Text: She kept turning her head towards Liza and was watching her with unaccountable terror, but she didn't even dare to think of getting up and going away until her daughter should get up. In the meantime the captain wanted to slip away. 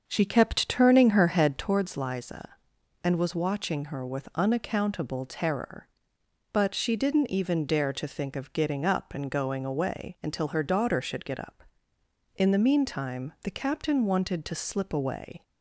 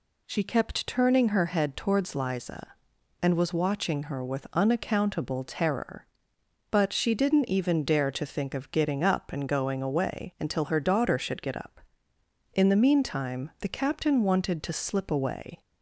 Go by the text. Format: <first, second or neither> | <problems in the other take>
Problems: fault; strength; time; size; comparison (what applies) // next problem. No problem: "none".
second | starts louder than the rest; until 1.8 s; 6.5 dB